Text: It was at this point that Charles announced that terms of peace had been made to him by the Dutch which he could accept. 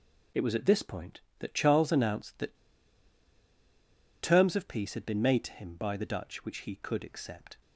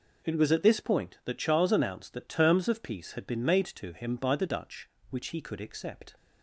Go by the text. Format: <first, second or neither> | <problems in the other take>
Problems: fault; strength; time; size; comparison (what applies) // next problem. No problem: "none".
second | pauses between "that" and "terms"; strong; at 2.5 s; 1.6 s long